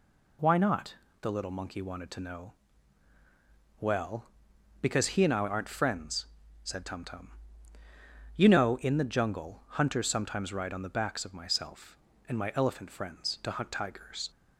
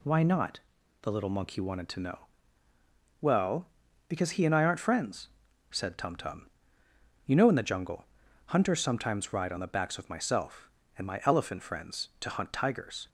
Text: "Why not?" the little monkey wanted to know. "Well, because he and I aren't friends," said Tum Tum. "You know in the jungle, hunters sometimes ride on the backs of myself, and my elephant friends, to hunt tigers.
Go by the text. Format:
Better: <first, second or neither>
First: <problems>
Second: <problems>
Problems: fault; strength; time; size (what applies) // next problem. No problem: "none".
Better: neither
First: none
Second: none